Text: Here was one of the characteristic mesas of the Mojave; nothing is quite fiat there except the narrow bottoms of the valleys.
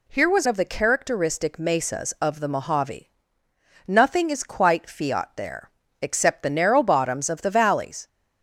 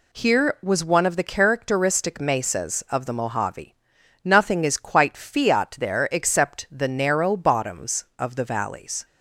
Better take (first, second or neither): second